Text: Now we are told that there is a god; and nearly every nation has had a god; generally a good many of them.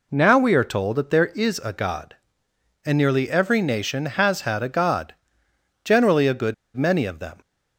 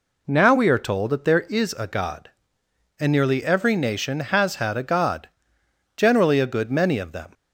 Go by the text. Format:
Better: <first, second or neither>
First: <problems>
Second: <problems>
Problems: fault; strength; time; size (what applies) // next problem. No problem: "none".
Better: second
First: pauses between "good" and "many"; slight; at 6.5 s; 0.21 s long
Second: none